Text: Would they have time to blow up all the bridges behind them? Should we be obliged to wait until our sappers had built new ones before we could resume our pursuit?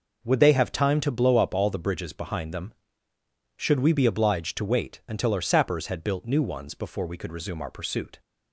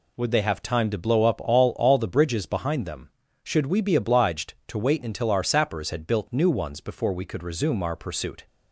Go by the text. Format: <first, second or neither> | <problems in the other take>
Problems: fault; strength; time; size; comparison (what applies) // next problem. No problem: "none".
first | says "all" twice; at 1.7 s